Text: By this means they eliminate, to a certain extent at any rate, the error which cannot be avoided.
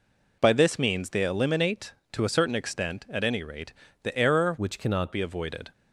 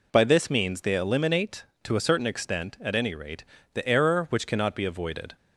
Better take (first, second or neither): second